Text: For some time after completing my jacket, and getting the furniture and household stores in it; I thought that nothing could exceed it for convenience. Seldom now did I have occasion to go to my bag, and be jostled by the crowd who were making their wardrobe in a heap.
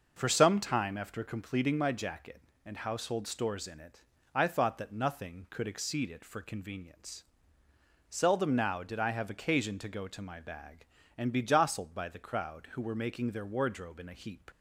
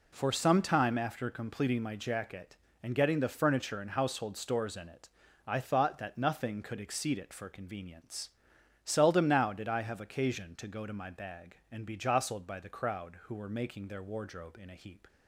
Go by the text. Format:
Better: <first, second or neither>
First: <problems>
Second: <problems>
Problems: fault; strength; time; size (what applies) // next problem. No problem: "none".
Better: second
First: skips "getting the furniture and"; at 2.7 s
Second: none